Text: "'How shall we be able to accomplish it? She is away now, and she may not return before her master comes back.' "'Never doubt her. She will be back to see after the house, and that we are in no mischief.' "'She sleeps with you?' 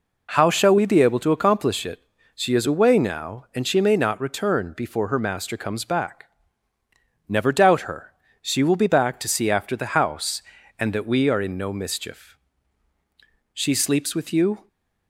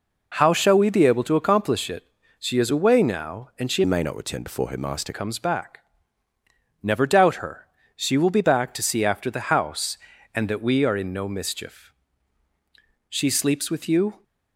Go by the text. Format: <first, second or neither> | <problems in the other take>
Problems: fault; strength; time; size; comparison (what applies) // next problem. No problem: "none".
first | changes voice from "may" to "master"; from 3.8 to 5.1 s; 1.3 s long